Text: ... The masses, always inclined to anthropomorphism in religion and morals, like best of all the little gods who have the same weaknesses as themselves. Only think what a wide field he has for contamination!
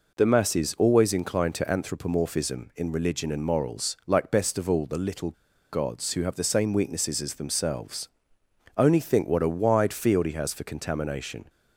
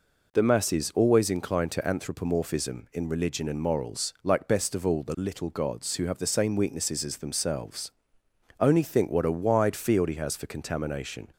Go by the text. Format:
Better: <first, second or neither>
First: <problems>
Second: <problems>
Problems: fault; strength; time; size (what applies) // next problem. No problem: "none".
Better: second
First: pauses between "little" and "gods"; at 5.3 s; 0.39 s long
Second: none